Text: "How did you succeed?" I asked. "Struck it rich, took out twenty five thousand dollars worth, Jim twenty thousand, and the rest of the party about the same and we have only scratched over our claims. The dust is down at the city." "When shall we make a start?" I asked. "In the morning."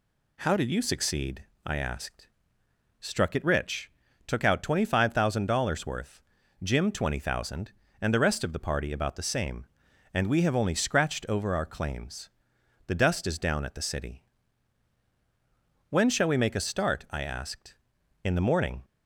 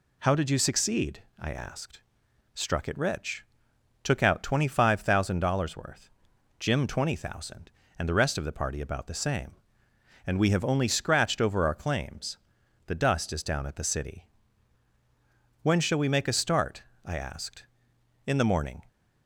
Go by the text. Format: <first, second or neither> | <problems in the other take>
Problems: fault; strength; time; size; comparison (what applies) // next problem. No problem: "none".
neither | none